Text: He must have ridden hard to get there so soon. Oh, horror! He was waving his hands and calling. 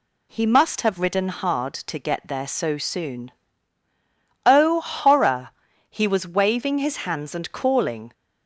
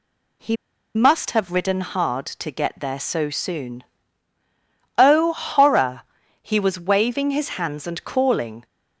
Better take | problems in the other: first | pauses between "He" and "must"; at 0.5 s; 0.39 s long

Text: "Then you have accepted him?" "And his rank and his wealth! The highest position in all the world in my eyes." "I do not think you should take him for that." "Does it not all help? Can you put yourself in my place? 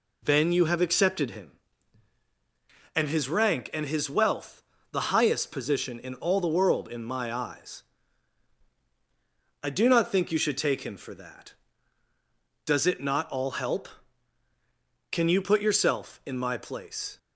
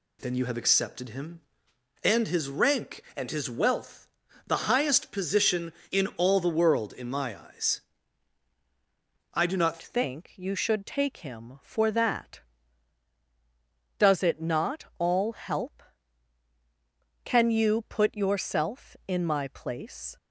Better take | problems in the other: first | changes voice at "think"; from 9.8 s on; 10.3 s long

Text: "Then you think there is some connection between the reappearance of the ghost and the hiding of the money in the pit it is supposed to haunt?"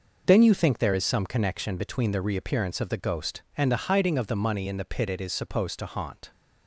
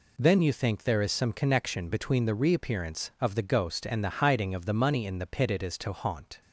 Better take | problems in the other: first | skips "supposed"; at 5.7 s

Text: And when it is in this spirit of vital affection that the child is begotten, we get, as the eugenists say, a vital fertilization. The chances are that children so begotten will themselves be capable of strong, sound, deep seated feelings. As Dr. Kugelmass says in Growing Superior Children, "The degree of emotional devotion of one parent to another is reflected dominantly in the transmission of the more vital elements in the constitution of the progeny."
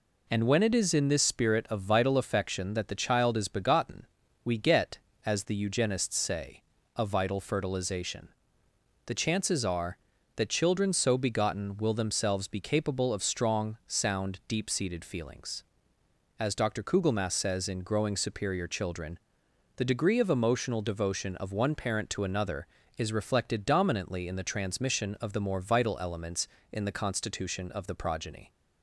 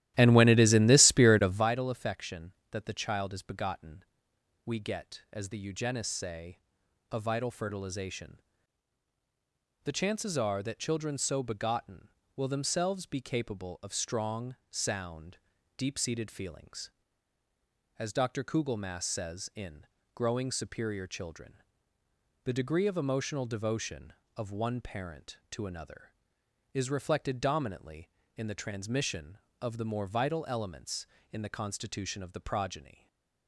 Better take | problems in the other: first | starts louder than the rest; strong; until 1.7 s; 13.5 dB // pauses between "in" and "Growing"; slight; at 19.8 s; 0.30 s long // stays silent after the last word; slight; from 32.9 s on; 0.5 s long

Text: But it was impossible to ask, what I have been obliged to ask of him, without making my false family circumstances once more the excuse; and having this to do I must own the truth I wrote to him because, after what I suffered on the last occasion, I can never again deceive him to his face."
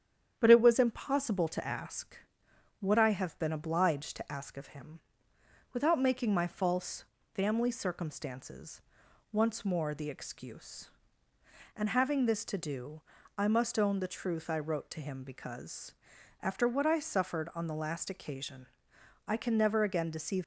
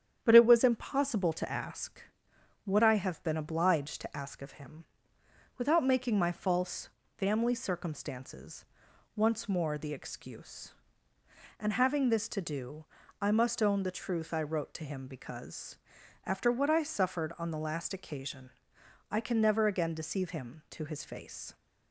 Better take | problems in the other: second | starts louder than the rest; strong; until 1.4 s; 9 dB; strong in the second // pauses between "false" and "family"; slight; at 7.0 s; 0.28 s long; slight in the second // pauses between "circumstances" and "once"; noticeable; at 8.8 s; 0.50 s long; noticeable in the second // pauses between "do" and "I"; slight; at 13.0 s; 0.36 s long; slight in the second // stops before "him to his face"; at 20.4 s

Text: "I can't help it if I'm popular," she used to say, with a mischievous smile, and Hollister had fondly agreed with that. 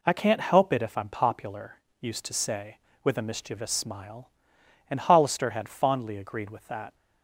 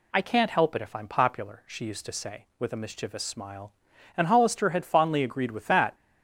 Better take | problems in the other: second | skips "she"; at 1.8 s

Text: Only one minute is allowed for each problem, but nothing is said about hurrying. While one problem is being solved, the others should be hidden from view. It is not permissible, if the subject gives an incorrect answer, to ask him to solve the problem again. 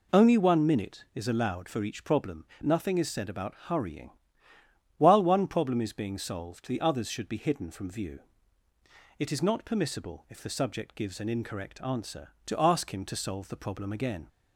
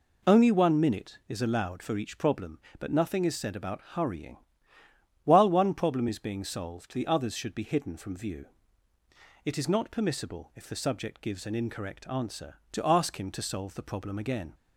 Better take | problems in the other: second | skips "but"; at 2.5 s

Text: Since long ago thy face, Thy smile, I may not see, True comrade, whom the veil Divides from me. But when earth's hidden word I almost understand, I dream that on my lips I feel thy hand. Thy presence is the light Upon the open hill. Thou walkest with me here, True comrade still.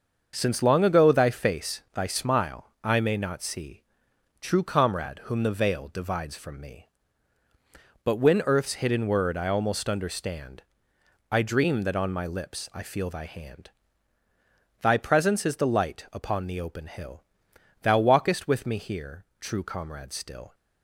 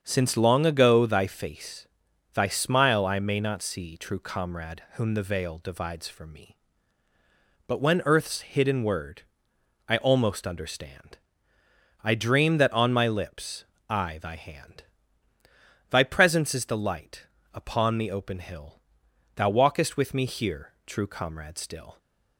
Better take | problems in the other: first | starts louder than the rest; until 1.0 s; 7 dB; also in the first // pauses between "word" and "I"; noticeable; at 9.2 s; 0.66 s long // pauses between "lips" and "I"; slight; at 13.6 s; 0.24 s long // skips "feel"; at 14.1 s // pauses between "light" and "Upon"; slight; at 17.2 s; 0.26 s long

